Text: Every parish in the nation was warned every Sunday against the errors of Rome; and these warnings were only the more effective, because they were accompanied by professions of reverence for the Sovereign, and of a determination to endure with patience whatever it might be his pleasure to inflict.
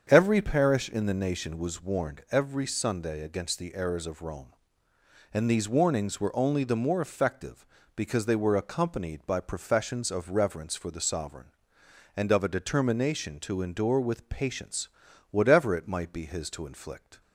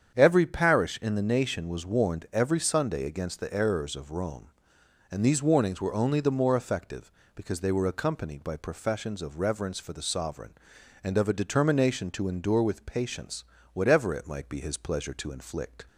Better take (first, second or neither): second